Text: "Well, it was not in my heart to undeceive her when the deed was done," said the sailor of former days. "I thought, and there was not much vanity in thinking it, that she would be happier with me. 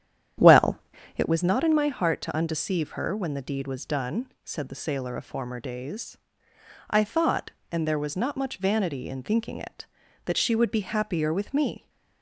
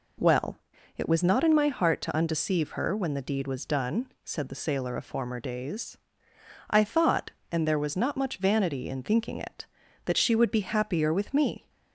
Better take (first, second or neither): second